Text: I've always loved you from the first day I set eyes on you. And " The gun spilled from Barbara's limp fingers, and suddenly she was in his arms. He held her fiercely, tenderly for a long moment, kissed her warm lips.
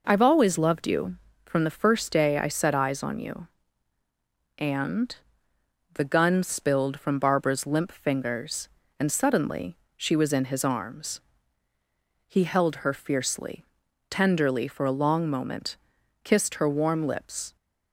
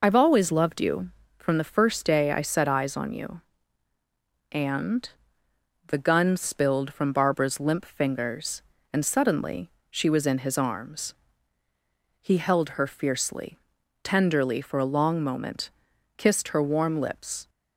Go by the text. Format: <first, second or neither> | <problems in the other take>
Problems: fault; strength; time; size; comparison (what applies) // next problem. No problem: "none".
first | loses the start of "I've"; at 0.0 s; 35 ms // pauses between "suddenly" and "she"; slight; at 9.7 s; 0.18 s long; slight in the first